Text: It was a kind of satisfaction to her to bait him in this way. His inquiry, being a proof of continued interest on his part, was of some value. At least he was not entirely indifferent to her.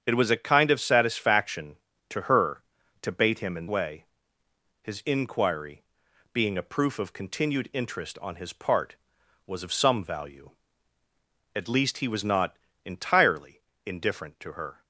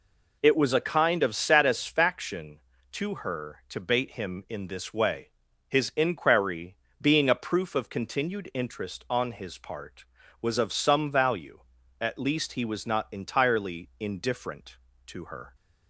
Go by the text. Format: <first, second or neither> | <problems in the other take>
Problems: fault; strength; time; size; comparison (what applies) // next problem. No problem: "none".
second | starts louder than the rest; strong; until 1.0 s; 8 dB // skips "this"; at 3.6 s // pauses between "not" and "entirely"; slight; at 12.5 s; 0.28 s long // pauses between "entirely" and "indifferent"; slight; at 13.6 s; 0.26 s long